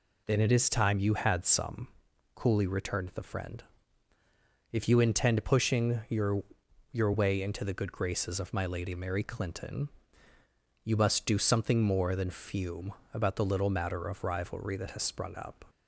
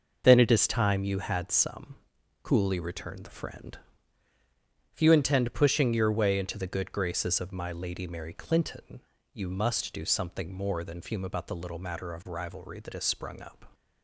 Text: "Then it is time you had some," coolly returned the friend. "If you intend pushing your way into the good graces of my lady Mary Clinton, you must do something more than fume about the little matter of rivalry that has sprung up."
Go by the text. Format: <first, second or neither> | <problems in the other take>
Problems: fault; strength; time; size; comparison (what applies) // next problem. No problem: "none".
second | says "your" twice; at 6.9 s // pauses between "fume" and "about"; slight; at 12.9 s; 0.22 s long